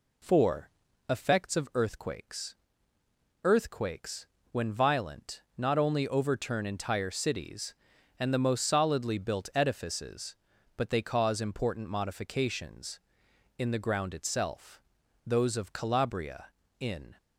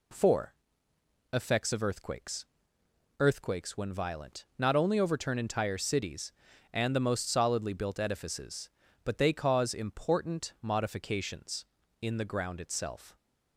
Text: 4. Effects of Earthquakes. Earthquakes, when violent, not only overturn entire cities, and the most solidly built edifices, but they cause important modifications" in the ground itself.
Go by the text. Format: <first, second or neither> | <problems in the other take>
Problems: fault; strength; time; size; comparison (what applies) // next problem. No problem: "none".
second | goes on to say "Those of Calabria in"; strong; from 15.2 s on; 1.9 s long